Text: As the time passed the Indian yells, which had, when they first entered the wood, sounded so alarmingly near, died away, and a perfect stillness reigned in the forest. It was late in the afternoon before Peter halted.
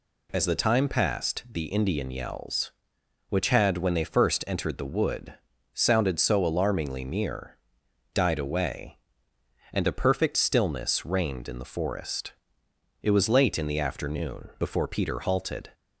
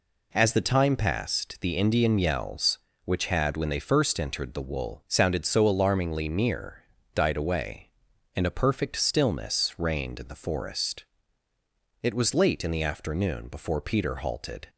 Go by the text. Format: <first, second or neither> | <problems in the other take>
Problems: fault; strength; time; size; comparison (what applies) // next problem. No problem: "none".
first | says "wool" for "wood"; at 4.6 s